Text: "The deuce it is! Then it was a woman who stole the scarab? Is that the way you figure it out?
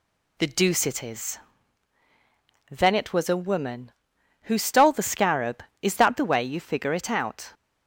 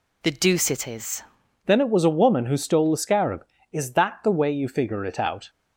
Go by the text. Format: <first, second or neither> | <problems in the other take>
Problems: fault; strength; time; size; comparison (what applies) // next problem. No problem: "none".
first | changes voice at "Then"; from 1.6 s on; 3.8 s long